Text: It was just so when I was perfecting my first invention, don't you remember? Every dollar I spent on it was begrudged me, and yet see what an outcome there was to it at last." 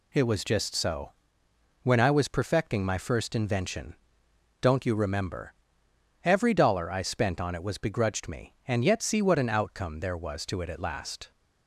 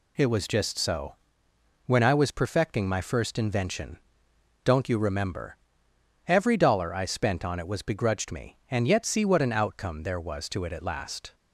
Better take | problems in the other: neither | pauses between "so" and "when"; noticeable; the same in both

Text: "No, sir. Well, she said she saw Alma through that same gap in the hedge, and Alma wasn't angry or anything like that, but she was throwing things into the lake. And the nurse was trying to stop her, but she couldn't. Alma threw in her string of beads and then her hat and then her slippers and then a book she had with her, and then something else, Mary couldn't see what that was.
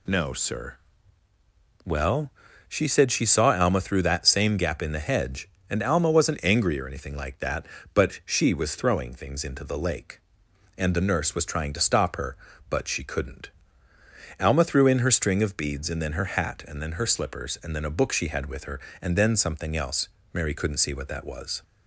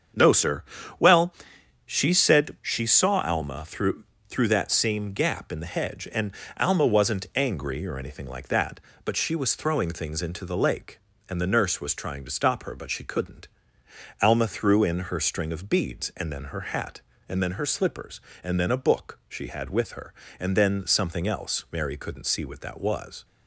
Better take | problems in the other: first | starts louder than the rest; strong; until 2.0 s; 7.5 dB // says "through" twice; at 4.2 s // pauses between "and" and "Alma"; slight; at 6.3 s; 0.24 s long

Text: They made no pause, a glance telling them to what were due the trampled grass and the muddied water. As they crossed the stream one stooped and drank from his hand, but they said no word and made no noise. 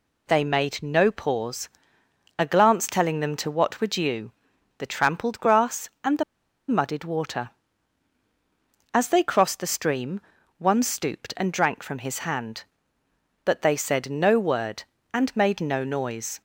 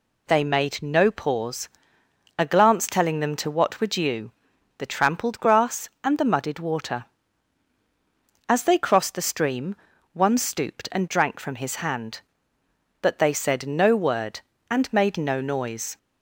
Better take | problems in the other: second | pauses between "due" and "the"; noticeable; at 4.3 s; 0.46 s long; noticeable in the second // pauses between "the" and "muddied"; at 6.2 s; 0.45 s long // pauses between "stream" and "one"; at 10.2 s; 0.38 s long; also in the second

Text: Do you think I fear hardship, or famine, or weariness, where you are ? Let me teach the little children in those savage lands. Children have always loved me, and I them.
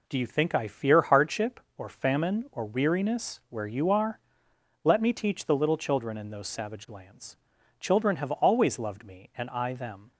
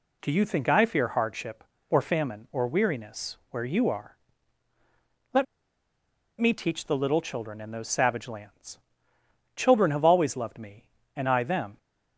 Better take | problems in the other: first | pauses between "Let" and "me"; noticeable; at 5.4 s; 0.96 s long

